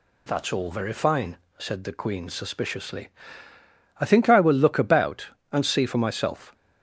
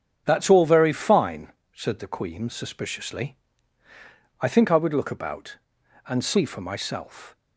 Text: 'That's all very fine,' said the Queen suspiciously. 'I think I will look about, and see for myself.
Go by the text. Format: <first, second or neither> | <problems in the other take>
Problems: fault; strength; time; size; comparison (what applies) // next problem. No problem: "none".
first | starts louder than the rest; strong; until 1.2 s; 8 dB // says "would" for "will"; at 4.7 s